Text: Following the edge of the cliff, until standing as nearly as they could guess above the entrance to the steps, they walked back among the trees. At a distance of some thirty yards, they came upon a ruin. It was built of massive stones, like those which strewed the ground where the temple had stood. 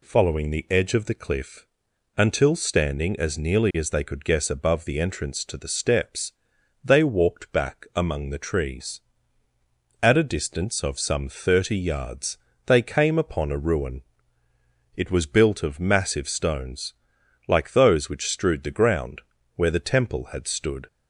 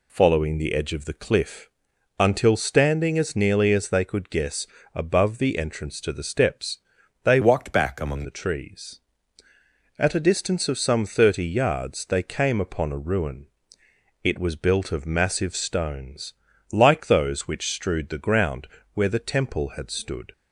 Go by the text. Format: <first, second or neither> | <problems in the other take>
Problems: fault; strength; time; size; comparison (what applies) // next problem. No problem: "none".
first | pauses between "guess" and "above"; slight; at 4.6 s; 0.26 s long // changes voice from "walked" to "among"; from 7.4 to 8.2 s; 0.8 s long // pauses between "ground" and "where"; slight; at 18.6 s; 0.28 s long; slight in the first